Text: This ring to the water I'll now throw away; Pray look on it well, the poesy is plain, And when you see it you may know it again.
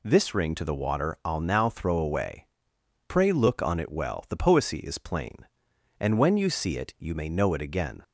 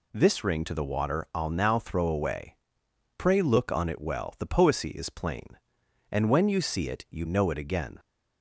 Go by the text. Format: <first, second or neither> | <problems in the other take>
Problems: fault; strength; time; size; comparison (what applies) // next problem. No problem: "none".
first | skips "may"; at 7.2 s